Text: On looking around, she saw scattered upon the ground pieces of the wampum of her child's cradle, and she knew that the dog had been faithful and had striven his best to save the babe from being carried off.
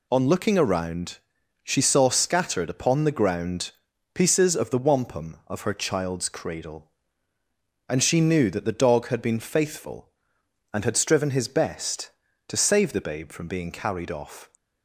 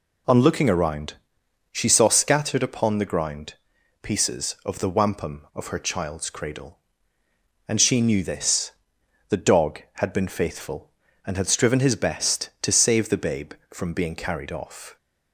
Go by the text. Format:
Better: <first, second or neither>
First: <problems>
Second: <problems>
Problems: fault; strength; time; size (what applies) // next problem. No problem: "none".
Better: first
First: pauses between "ground" and "pieces"; at 3.7 s; 0.42 s long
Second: pauses between "ground" and "pieces"; noticeable; at 3.5 s; 0.46 s long // says "this" for "that"; at 8.2 s